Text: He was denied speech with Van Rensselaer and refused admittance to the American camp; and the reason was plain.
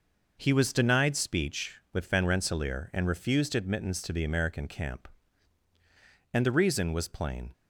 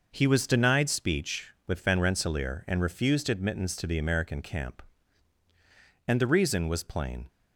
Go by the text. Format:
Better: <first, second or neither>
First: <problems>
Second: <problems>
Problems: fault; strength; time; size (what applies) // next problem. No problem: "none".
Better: neither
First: none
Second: none